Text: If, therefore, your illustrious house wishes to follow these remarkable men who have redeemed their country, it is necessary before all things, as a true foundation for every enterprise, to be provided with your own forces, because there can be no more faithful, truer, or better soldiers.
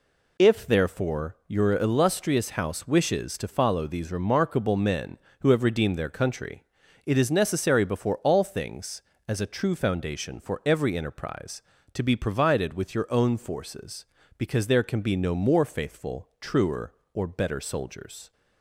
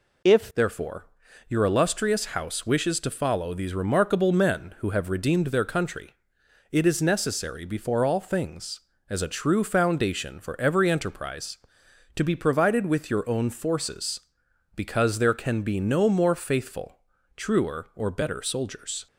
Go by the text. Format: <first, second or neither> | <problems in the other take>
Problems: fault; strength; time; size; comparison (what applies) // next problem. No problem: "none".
first | changes voice at "therefore"; from 0.5 s on; 18.5 s long